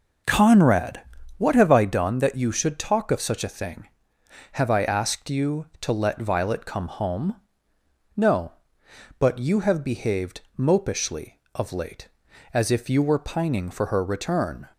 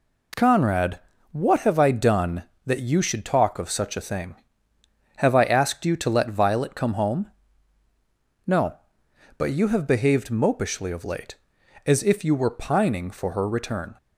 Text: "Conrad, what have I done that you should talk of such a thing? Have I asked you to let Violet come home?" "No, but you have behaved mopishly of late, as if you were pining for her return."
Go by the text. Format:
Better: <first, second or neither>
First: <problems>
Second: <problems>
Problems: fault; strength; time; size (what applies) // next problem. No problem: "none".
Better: second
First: starts louder than the rest; noticeable; until 1.9 s; 5.5 dB // pauses between "behaved" and "mopishly"; slight; at 10.3 s; 0.16 s long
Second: none